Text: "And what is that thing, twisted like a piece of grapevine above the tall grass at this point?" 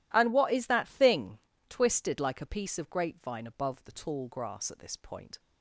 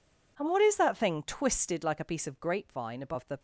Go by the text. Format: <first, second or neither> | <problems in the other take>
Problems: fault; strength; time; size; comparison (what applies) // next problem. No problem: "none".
first | stops before "tall grass at this point"; at 3.3 s